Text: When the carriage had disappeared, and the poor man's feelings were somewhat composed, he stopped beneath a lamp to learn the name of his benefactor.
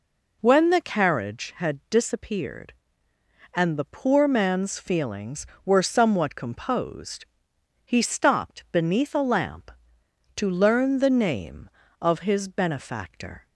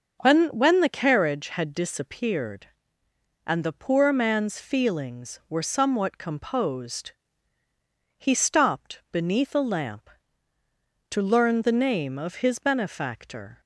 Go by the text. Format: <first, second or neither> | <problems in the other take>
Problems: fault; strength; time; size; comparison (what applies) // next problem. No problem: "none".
first | starts louder than the rest; until 1.2 s; 6 dB // says "When" twice; at 0.4 s